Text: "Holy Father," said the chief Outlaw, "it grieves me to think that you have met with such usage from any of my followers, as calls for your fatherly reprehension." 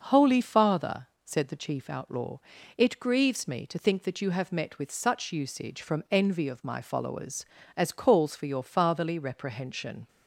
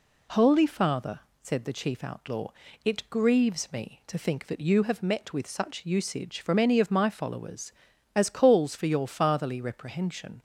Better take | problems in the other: second | says "envy" for "any"; at 6.0 s

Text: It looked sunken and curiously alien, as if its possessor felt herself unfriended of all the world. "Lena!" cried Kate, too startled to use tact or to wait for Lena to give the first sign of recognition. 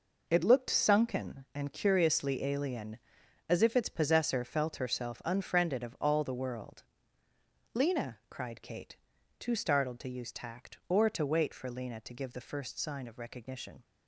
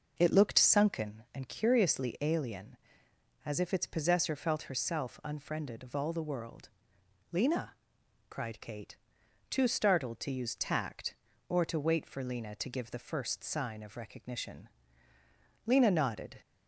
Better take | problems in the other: first | goes on to say "Lena nodded"; noticeable; from 15.6 s on; 0.72 s long

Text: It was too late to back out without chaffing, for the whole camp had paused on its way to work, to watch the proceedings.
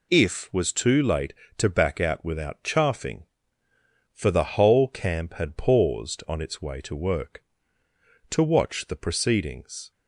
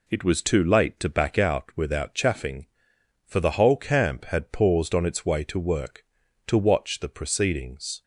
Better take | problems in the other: second | says "If" for "It"; at 0.1 s

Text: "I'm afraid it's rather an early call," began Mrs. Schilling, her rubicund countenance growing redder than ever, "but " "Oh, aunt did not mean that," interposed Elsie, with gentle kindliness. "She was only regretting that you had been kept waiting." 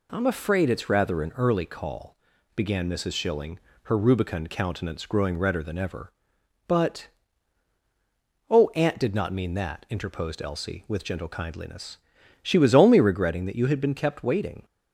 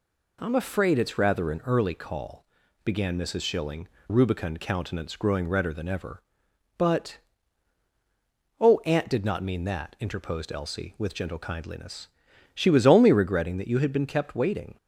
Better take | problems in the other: first | skips "her"; at 3.9 s

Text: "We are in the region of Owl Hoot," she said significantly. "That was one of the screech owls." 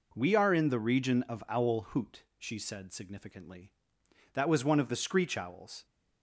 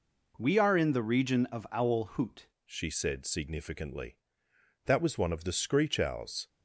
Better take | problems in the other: first | changes voice at "she"; from 2.6 s on; 3.8 s long

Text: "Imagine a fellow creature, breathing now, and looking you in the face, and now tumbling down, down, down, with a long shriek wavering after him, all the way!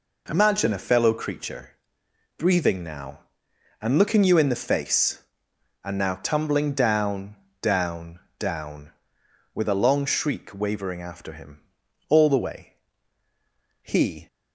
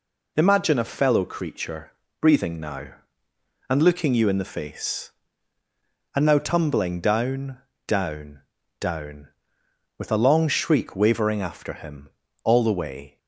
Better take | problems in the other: second | goes on to say "He"; slight; from 13.8 s on; 0.44 s long

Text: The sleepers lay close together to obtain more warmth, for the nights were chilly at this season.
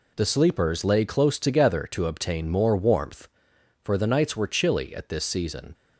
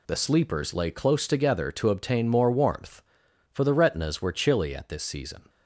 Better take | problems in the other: first | says "retinas" for "nights"; at 3.7 s

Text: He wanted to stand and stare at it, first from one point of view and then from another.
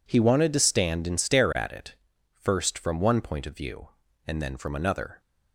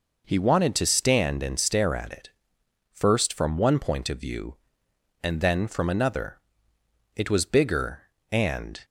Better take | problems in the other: first | goes on to say "It was bigger and"; strong; from 7.1 s on; 1.6 s long

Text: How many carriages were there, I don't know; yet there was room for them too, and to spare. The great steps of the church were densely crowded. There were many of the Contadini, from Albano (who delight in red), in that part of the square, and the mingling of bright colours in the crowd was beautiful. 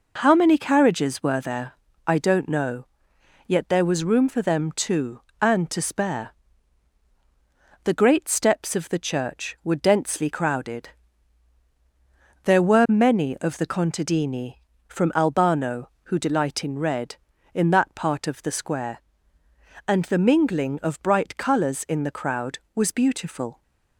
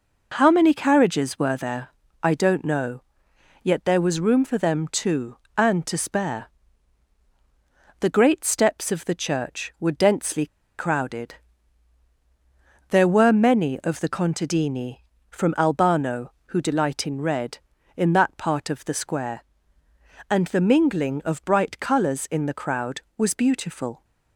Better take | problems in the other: first | pauses between "densely" and "crowded"; slight; at 10.4 s; 0.31 s long

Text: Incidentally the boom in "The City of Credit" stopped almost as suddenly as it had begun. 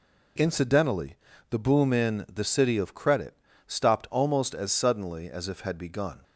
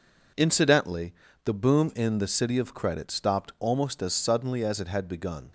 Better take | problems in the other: second | pauses between "Incidentally" and "the"; slight; at 1.1 s; 0.34 s long; slight in the second // pauses between "Credit" and "stopped"; slight; at 3.3 s; 0.30 s long // says "if" for "it"; at 5.4 s

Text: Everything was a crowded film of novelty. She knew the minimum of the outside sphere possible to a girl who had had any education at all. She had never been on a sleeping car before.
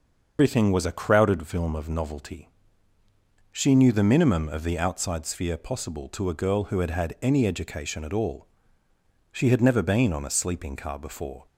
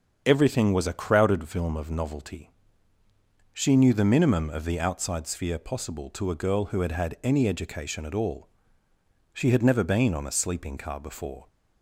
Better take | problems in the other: second | loses the start of "Everything"; at 0.3 s; 145 ms // starts louder than the rest; until 1.3 s; 6.5 dB; strong in the second

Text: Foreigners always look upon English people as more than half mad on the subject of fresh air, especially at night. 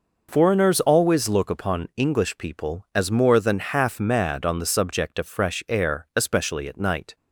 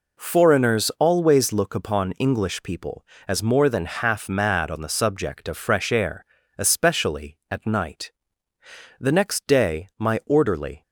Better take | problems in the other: first | goes on to say "The next day my orderly"; strong; from 8.9 s on; 1.8 s long

